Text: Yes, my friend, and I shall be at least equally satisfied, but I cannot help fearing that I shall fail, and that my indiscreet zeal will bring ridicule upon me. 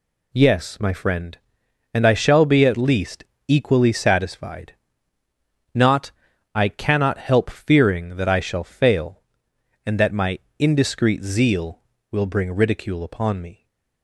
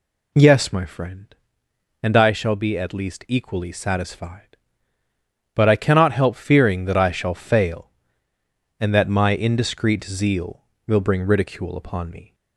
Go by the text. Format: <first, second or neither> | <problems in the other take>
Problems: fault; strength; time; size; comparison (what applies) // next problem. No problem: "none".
second | pauses between "least" and "equally"; slight; at 3.2 s; 0.24 s long // says "not" for "but"; at 5.7 s // pauses between "my" and "indiscreet"; slight; at 10.3 s; 0.20 s long